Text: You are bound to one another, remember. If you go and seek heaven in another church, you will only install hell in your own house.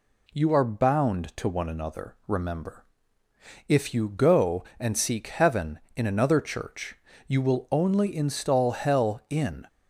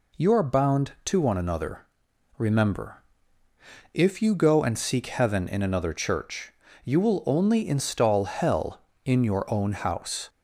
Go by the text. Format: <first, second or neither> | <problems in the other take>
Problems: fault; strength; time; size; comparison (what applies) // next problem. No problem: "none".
second | stops before "your own house"; at 9.6 s